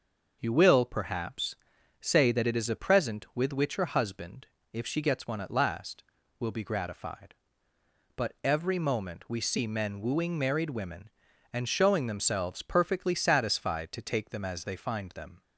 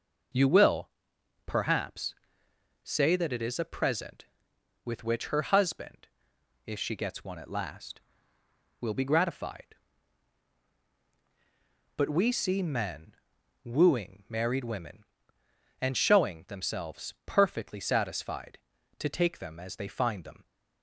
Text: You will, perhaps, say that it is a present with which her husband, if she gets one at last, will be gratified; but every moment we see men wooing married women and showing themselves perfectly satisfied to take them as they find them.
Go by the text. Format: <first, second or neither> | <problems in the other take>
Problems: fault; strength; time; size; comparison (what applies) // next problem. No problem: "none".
first | skips "every moment"; at 12.0 s // pauses between "men" and "wooing"; noticeable; at 13.1 s; 0.48 s long